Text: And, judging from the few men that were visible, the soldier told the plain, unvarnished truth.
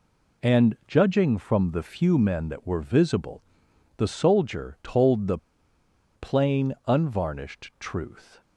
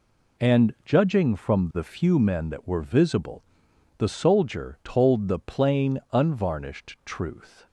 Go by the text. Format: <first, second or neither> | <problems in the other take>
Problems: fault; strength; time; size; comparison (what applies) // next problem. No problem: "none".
second | pauses between "the" and "plain"; noticeable; at 5.3 s; 0.78 s long